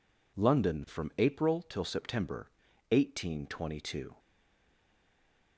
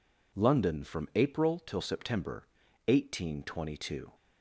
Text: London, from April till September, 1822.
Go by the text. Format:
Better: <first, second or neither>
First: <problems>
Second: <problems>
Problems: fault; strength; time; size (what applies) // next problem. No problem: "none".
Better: second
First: stays silent after the last word; noticeable; from 4.1 s on; 1.4 s long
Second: none